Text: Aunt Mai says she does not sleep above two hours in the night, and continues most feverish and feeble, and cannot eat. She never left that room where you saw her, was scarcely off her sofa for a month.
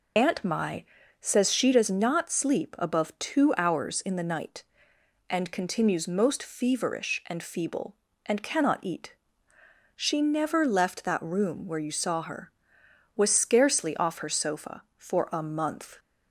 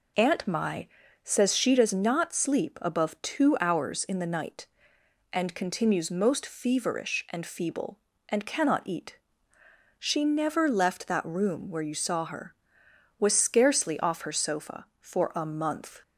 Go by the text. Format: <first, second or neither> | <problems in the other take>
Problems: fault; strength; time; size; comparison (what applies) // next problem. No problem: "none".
second | loses the start of "Aunt"; at 0.1 s; 30 ms // pauses between "Mai" and "says"; slight; at 0.8 s; 0.36 s long; slight in the second